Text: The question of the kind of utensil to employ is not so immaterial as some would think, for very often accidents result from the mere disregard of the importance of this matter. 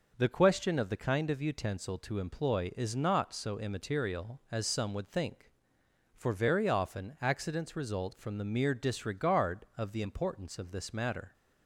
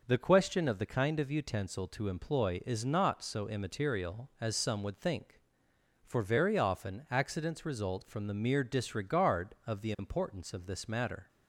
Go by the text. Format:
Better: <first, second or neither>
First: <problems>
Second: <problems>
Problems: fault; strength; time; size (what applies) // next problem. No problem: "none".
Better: neither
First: none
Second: none